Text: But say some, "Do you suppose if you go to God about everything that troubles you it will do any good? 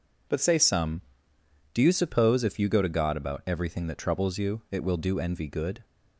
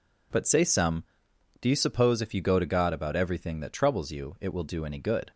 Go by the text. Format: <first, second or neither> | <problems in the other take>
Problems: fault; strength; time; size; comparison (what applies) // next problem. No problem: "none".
second | says "envy" for "any"; at 5.2 s